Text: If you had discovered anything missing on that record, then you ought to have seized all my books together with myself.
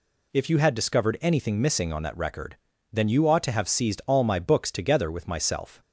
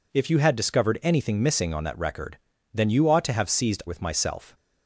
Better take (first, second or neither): first